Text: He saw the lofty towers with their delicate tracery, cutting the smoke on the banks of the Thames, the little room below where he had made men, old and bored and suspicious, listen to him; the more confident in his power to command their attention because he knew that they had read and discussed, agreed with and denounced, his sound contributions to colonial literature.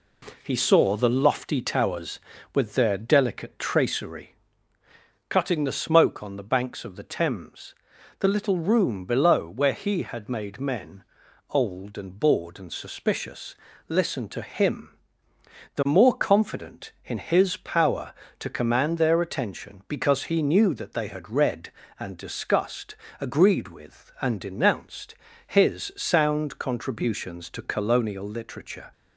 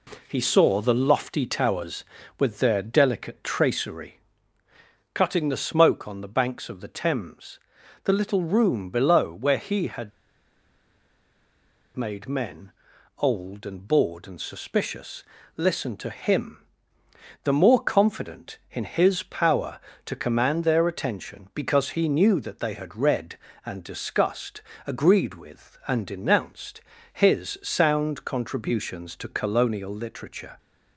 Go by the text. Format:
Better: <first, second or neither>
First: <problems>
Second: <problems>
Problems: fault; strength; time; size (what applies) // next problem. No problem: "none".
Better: first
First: none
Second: pauses between "had" and "made"; strong; at 10.1 s; 1.8 s long